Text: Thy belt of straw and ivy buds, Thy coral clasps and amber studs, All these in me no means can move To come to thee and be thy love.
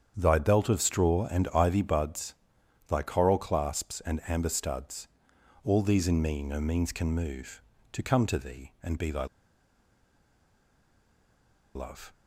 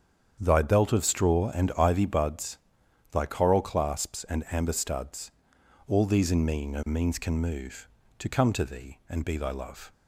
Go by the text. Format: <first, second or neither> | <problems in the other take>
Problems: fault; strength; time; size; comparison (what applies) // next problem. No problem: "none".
second | starts louder than the rest; strong; until 1.1 s; 8 dB; strong in the second // pauses between "thy" and "love"; strong; at 9.2 s; 2.4 s long